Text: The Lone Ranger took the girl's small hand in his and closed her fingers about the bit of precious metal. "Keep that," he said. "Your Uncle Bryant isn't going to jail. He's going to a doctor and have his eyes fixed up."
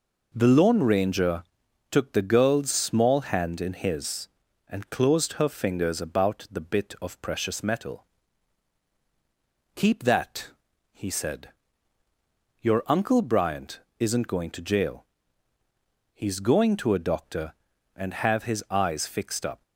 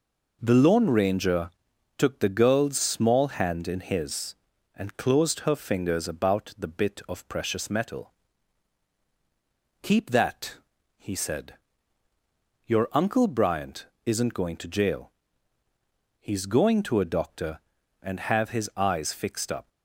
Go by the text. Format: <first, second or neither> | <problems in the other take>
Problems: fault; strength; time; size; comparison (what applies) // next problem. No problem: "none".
neither | pauses between "Ranger" and "took"; noticeable; the same in both // pauses between "Bryant" and "isn't"; slight; the same in both